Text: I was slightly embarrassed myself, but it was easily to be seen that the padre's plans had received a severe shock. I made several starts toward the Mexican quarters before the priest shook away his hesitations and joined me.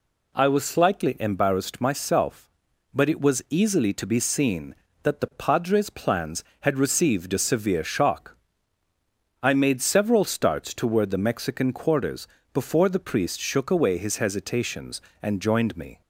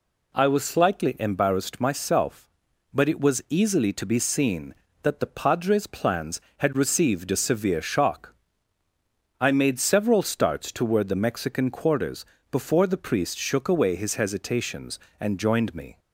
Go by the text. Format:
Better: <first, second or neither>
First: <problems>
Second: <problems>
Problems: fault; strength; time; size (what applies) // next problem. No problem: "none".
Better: neither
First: pauses between "quarters" and "before"; slight; at 12.2 s; 0.26 s long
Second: pauses between "quarters" and "before"; slight; at 12.2 s; 0.26 s long